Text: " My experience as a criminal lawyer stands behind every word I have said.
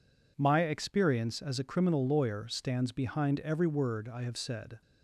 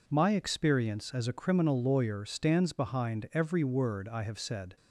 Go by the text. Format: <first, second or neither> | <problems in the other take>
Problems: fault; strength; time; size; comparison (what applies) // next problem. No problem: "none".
neither | none